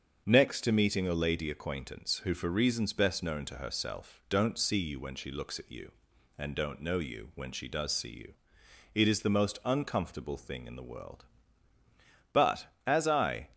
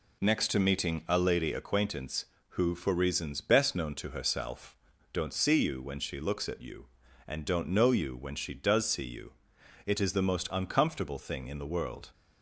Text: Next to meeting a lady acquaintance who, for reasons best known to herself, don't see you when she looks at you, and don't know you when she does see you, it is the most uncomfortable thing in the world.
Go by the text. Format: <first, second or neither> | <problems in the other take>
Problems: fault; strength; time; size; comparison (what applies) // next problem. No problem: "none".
second | starts louder than the rest; until 1.2 s; 7 dB // goes on to say "But as I"; noticeable; from 12.3 s on; 1.1 s long